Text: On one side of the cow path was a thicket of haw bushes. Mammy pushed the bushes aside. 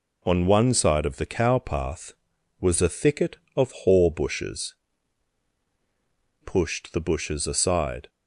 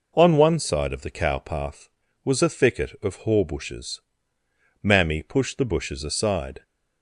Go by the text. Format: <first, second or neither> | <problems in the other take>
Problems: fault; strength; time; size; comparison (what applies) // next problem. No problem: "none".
second | skips "Mammy"; at 5.5 s